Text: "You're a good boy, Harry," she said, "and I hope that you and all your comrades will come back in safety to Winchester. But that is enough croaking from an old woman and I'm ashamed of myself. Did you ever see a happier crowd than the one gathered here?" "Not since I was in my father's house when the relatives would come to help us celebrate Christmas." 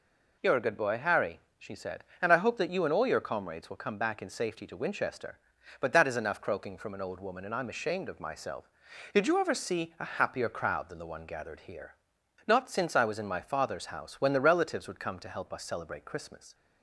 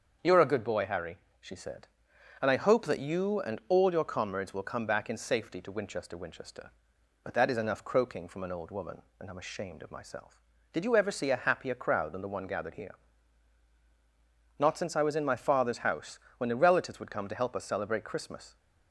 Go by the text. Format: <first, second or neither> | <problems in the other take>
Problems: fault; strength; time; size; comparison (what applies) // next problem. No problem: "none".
first | starts louder than the rest; until 1.4 s; 7 dB // says "Winchester" twice; at 6.1 s // pauses between "house" and "when"; slight; at 16.1 s; 0.18 s long